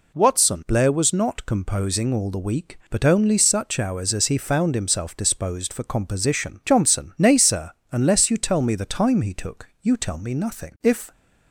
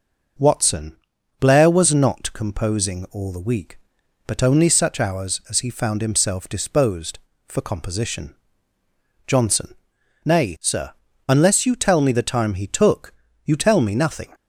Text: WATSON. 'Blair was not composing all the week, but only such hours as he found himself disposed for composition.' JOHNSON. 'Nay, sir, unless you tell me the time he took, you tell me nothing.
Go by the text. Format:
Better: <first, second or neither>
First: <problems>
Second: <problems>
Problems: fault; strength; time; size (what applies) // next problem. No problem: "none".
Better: second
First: goes on to say "If"; slight; from 10.8 s on; 0.28 s long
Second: none